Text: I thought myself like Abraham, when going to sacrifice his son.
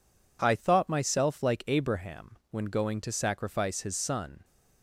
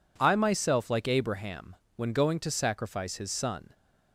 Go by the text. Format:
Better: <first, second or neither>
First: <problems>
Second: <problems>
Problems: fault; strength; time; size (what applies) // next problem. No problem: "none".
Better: first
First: none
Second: skips "thought"; at 0.3 s